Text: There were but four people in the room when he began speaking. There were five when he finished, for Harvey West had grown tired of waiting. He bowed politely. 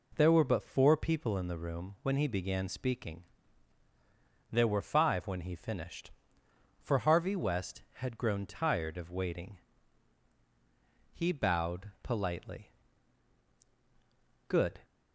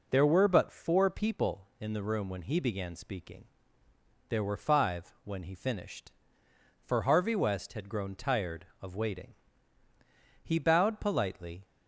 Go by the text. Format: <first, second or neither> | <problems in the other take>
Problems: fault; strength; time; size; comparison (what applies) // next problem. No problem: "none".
second | goes on to say "Good"; slight; from 14.4 s on; 0.34 s long